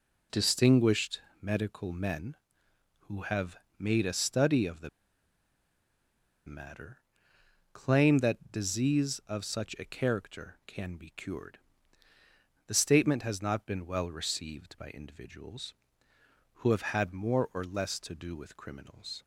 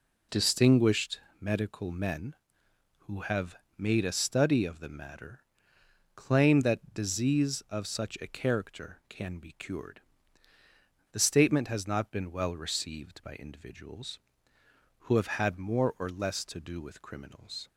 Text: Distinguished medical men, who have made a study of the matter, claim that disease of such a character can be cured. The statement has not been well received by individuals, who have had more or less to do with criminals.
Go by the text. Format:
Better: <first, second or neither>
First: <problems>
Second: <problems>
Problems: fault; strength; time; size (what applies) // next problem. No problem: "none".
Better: second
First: pauses between "Distinguished" and "medical"; slight; at 1.2 s; 0.20 s long // pauses between "have" and "made"; slight; at 3.5 s; 0.24 s long // pauses between "the" and "matter"; strong; at 4.8 s; 1.5 s long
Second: pauses between "Distinguished" and "medical"; slight; at 1.2 s; 0.20 s long // pauses between "have" and "made"; slight; at 3.5 s; 0.24 s long